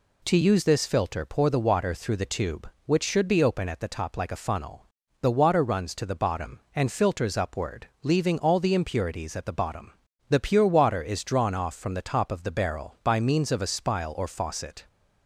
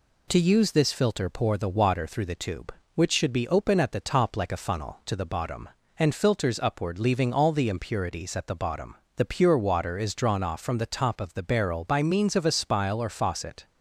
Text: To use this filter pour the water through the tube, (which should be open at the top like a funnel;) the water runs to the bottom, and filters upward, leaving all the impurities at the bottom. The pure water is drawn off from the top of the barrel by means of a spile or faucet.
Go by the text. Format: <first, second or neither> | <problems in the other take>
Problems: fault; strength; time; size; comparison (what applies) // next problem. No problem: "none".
first | skips "the water runs"; at 5.0 s